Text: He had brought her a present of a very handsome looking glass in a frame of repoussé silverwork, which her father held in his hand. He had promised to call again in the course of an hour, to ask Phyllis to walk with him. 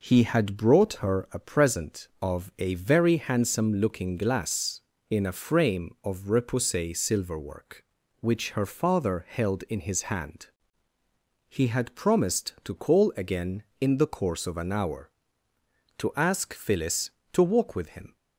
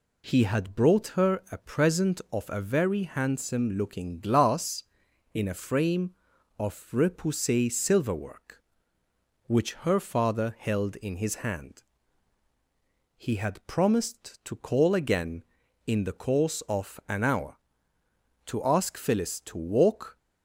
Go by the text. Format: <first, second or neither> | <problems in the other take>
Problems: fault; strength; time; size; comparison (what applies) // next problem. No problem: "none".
first | stops before "with him"; at 20.1 s